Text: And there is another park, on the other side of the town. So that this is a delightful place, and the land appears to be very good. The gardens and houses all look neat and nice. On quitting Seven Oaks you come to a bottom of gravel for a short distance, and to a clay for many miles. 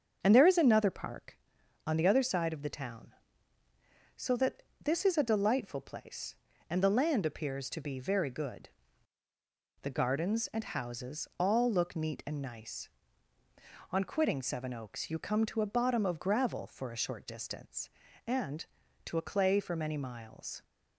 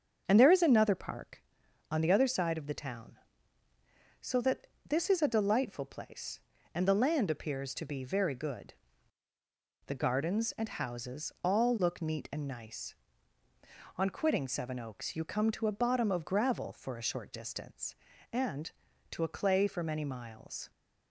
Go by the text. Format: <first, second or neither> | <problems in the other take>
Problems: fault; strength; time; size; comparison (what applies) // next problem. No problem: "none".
neither | starts louder than the rest; the same in both // pauses between "that" and "this"; slight; the same in both